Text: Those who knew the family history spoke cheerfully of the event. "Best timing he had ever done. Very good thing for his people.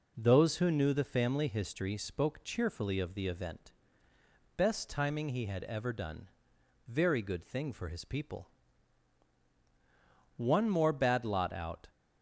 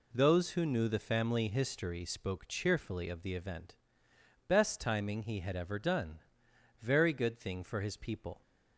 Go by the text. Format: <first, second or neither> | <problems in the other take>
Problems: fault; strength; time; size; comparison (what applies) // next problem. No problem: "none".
second | goes on to say "One more bad lot out"; from 10.3 s on; 1.5 s long